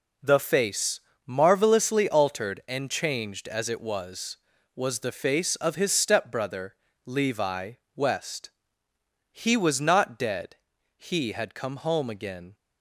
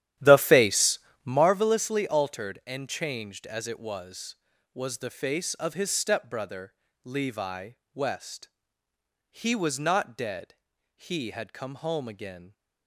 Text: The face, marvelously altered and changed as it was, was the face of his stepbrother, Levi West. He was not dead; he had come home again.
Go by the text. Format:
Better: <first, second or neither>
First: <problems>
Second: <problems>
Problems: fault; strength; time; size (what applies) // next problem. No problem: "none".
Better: first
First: pauses between "Levi" and "West"; slight; at 7.7 s; 0.22 s long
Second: starts louder than the rest; strong; until 1.5 s; 11.5 dB // pauses between "Levi" and "West"; slight; at 7.7 s; 0.22 s long